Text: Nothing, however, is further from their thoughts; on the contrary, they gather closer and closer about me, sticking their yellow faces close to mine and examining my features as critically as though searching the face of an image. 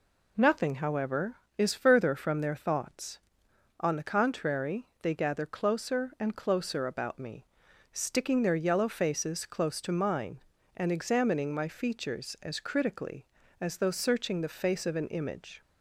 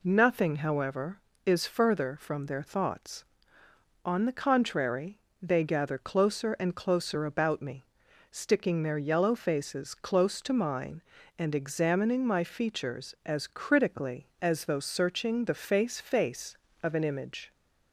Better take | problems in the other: first | says "face" twice; at 16.0 s

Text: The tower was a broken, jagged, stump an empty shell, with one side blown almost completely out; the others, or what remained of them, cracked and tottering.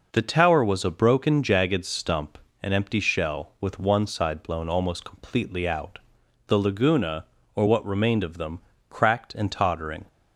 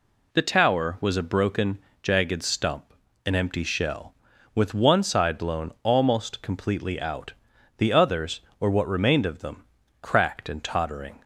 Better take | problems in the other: second | pauses between "stump" and "an"; slight; at 2.3 s; 0.24 s long; slight in the second // says "laguna" for "others"; at 6.5 s

